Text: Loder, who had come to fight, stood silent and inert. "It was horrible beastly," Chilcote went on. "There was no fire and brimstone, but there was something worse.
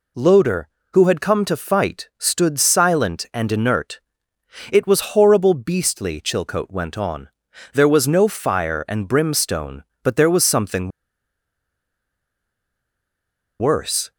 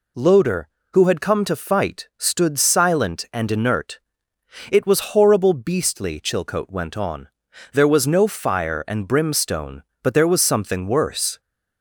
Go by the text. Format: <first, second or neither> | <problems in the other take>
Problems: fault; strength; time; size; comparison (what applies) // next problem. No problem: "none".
second | pauses between "something" and "worse"; strong; at 10.9 s; 2.6 s long